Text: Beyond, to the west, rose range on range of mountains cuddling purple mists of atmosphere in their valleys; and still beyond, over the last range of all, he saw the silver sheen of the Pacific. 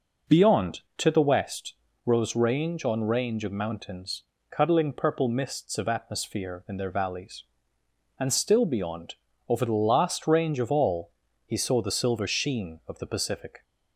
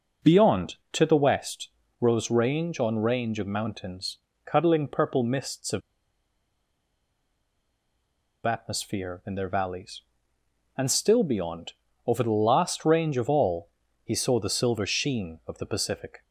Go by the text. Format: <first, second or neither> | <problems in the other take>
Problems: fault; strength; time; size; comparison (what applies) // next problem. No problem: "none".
first | pauses between "mountains" and "cuddling"; slight; at 4.1 s; 0.26 s long; slight in the first // pauses between "of" and "atmosphere"; strong; at 5.8 s; 2.6 s long